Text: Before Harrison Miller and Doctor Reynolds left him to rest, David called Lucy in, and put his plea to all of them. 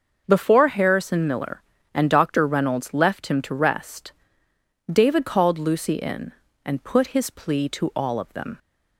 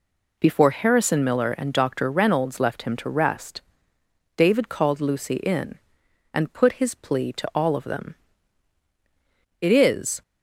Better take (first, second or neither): first